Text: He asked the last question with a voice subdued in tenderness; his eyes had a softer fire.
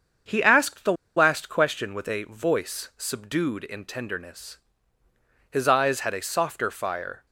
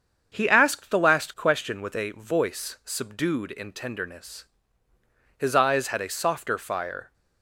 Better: second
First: starts louder than the rest; until 1.5 s; 7 dB // pauses between "the" and "last"; slight; at 0.9 s; 0.23 s long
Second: starts louder than the rest; strong; until 1.3 s; 7 dB

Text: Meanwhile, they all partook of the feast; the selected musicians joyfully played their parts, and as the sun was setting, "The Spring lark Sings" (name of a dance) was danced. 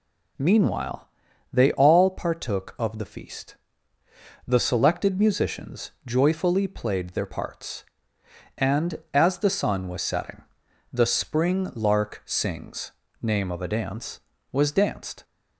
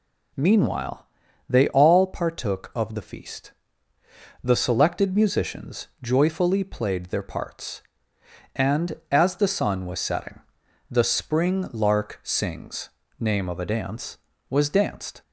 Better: neither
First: none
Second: none

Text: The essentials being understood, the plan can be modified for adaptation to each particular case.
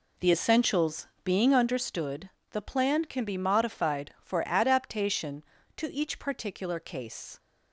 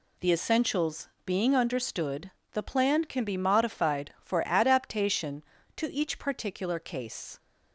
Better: second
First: starts louder than the rest; slight; until 1.9 s; 3 dB // pauses between "essentials" and "being"; slight; at 1.0 s; 0.16 s long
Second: pauses between "essentials" and "being"; slight; at 1.0 s; 0.16 s long

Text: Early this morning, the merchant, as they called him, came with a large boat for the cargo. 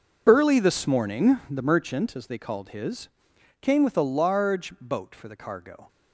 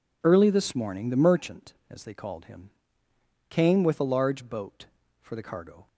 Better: second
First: says "his" for "him"; at 2.6 s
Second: none

